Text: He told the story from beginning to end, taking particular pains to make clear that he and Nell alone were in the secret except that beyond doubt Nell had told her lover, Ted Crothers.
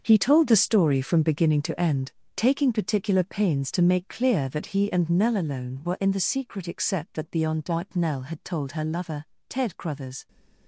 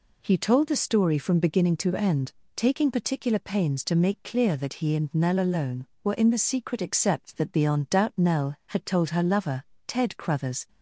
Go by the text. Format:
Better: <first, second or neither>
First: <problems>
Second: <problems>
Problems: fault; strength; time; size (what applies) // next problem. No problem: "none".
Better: second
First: gets quieter; strong; throughout; 13 dB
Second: none